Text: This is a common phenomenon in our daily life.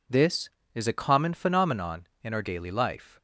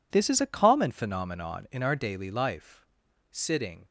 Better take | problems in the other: first | goes on to say "Sitting"; from 3.3 s on; 0.54 s long

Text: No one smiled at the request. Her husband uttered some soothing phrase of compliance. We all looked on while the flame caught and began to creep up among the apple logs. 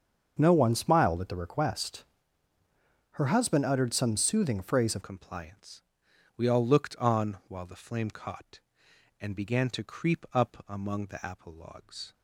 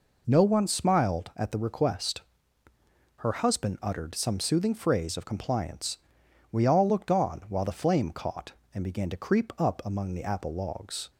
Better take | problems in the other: second | starts louder than the rest; until 1.4 s; 7 dB // changes voice at "compliance"; from 5.0 s on; 7.1 s long

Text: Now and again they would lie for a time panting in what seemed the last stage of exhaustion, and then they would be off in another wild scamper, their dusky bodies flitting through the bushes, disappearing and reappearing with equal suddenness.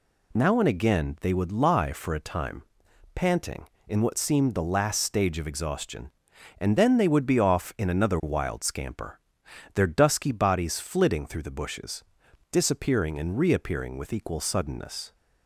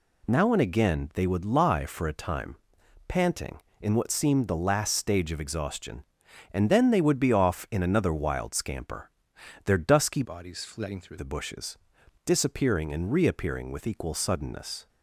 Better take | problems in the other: first | pauses between "time" and "panting"; noticeable; at 2.5 s; 0.50 s long; noticeable in the first // changes voice from "bodies" to "through"; from 10.2 to 11.1 s; 0.9 s long

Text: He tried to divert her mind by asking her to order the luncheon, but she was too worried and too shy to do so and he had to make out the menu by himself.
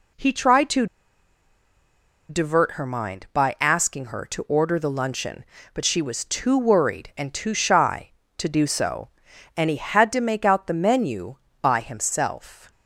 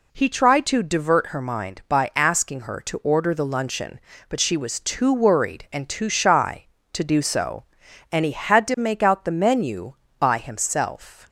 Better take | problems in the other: second | pauses between "to" and "divert"; strong; at 0.8 s; 1.4 s long

